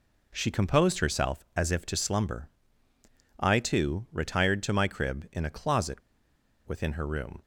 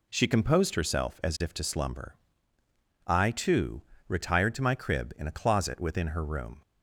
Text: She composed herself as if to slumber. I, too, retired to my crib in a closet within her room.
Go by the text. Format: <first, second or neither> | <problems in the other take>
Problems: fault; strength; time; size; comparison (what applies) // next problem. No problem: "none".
second | pauses between "closet" and "within"; noticeable; at 6.0 s; 0.67 s long